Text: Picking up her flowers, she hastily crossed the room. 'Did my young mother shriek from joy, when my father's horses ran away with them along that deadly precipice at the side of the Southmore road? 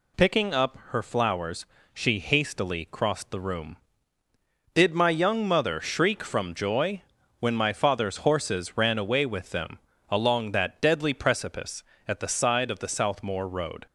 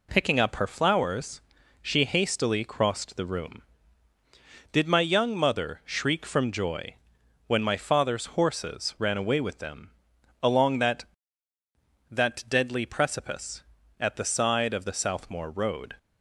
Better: first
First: pauses between "them" and "along"; slight; at 9.7 s; 0.32 s long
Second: pauses between "them" and "along"; noticeable; at 9.9 s; 0.50 s long // says "that" twice; at 12.0 s

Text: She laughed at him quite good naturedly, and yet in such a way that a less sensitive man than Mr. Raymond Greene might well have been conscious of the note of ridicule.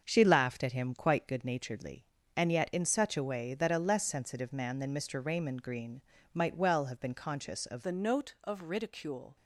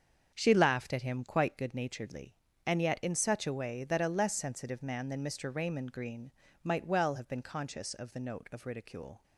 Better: second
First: starts louder than the rest; until 1.0 s; 6.5 dB // pauses between "Greene" and "might"; slight; at 6.0 s; 0.32 s long // changes voice at "the"; from 7.8 s on; 1.5 s long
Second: starts louder than the rest; until 1.3 s; 7 dB // pauses between "Greene" and "might"; slight; at 6.3 s; 0.32 s long

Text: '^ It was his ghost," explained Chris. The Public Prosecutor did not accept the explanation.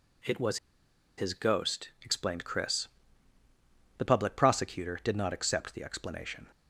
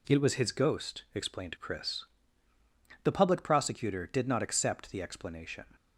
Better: second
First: pauses between "was" and "his"; noticeable; at 0.5 s; 0.59 s long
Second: none

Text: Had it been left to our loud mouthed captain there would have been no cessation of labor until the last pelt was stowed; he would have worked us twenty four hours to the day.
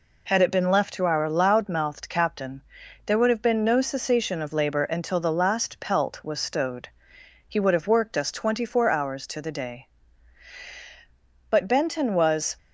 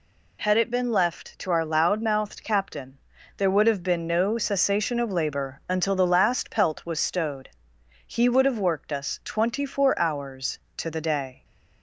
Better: second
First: pauses between "captain" and "there"; at 2.6 s; 0.44 s long // goes on to say "But Benton was"; noticeable; from 11.4 s on; 1.0 s long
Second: pauses between "captain" and "there"; at 2.9 s; 0.40 s long

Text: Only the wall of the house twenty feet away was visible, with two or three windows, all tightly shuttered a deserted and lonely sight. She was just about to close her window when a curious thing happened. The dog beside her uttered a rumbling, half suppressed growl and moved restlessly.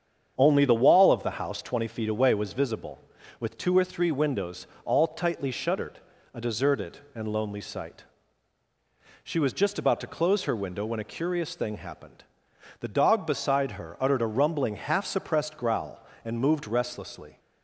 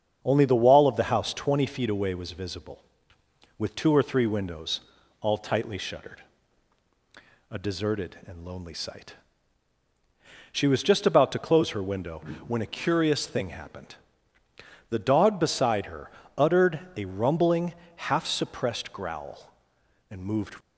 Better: first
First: starts louder than the rest; strong; until 1.3 s; 8 dB // pauses between "shuttered" and "a"; slight; at 5.9 s; 0.36 s long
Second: starts louder than the rest; strong; until 1.2 s; 7.5 dB // pauses between "shuttered" and "a"; strong; at 6.2 s; 1.3 s long // pauses between "window" and "when"; slight; at 12.2 s; 0.26 s long // pauses between "her" and "uttered"; slight; at 16.0 s; 0.28 s long // pauses between "uttered" and "a"; slight; at 16.7 s; 0.16 s long // stops before "restlessly"; at 20.6 s

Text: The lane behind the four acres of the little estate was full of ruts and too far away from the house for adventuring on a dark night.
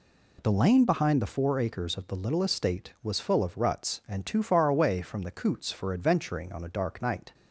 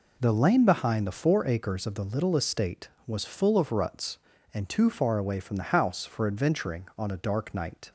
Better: second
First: says "coots" for "house"; at 5.3 s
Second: none

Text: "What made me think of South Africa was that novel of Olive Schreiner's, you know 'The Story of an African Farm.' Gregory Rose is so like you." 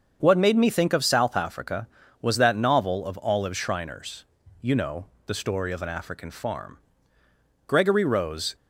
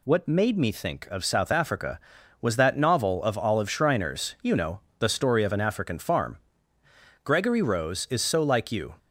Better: second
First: starts louder than the rest; until 1.2 s; 7 dB // pauses between "know" and "The"; slight; at 5.0 s; 0.18 s long // stops before "is so like you"; at 8.5 s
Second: pauses between "know" and "The"; slight; at 4.7 s; 0.18 s long

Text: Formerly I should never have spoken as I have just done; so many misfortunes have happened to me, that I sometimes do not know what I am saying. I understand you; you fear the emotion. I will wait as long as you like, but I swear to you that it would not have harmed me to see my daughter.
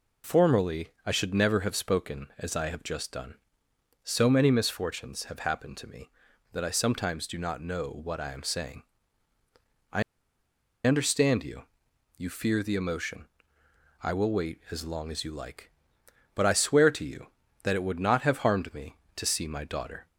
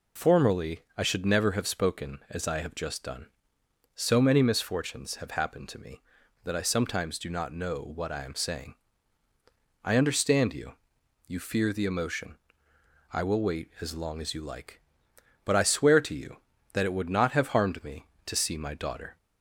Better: second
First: pauses between "Formerly" and "I"; slight; at 0.8 s; 0.16 s long // pauses between "I" and "understand"; noticeable; at 10.0 s; 0.84 s long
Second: pauses between "Formerly" and "I"; slight; at 0.8 s; 0.16 s long

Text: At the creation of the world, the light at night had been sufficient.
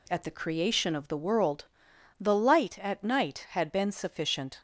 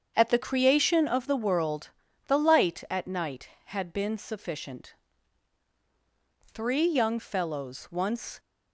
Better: first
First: none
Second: starts louder than the rest; strong; until 1.1 s; 7.5 dB // goes on to say "Three young fellows once"; strong; from 6.5 s on; 1.8 s long

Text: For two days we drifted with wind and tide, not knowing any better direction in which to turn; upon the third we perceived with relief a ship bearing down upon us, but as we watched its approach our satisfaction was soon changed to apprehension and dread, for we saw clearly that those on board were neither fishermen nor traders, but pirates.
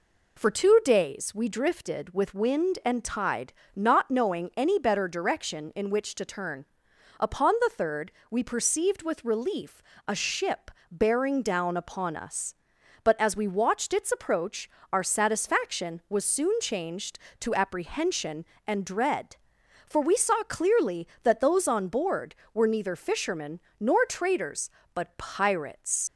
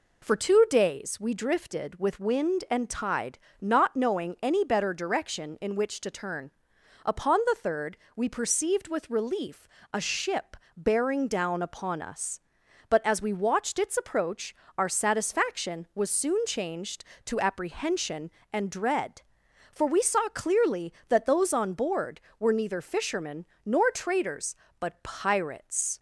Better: second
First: pauses between "third" and "we"; slight; at 8.1 s; 0.18 s long // pauses between "relief" and "a"; slight; at 9.8 s; 0.26 s long // pauses between "ship" and "bearing"; slight; at 10.6 s; 0.22 s long // pauses between "approach" and "our"; slight; at 14.6 s; 0.22 s long // pauses between "fishermen" and "nor"; slight; at 23.5 s; 0.20 s long // leaves "pirates" unfinished; at 26.0 s; 60 ms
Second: pauses between "third" and "we"; slight; at 7.9 s; 0.18 s long // pauses between "relief" and "a"; slight; at 9.6 s; 0.26 s long // pauses between "ship" and "bearing"; slight; at 10.5 s; 0.22 s long // pauses between "approach" and "our"; slight; at 14.5 s; 0.22 s long // pauses between "fishermen" and "nor"; slight; at 23.4 s; 0.20 s long

